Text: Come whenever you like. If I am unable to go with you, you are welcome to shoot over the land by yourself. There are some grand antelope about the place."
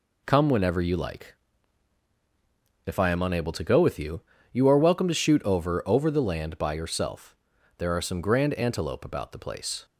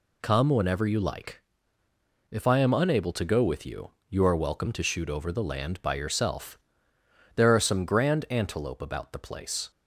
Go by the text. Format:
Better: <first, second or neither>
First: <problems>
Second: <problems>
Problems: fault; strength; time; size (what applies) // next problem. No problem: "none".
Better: second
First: says "over" twice; at 5.8 s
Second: none